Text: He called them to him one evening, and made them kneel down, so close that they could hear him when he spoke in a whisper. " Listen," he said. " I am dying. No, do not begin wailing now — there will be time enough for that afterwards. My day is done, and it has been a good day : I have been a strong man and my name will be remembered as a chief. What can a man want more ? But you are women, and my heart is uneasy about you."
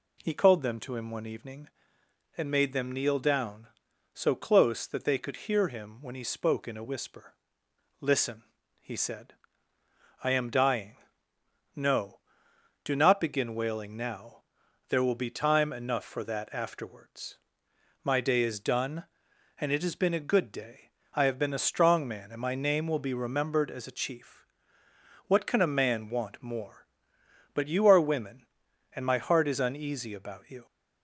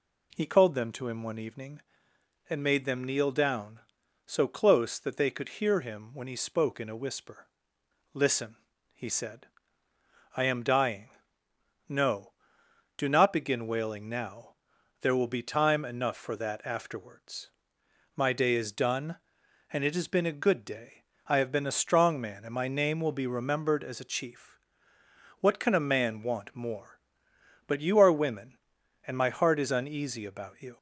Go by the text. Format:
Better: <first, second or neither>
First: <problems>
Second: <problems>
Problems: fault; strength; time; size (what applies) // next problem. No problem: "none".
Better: neither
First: none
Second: none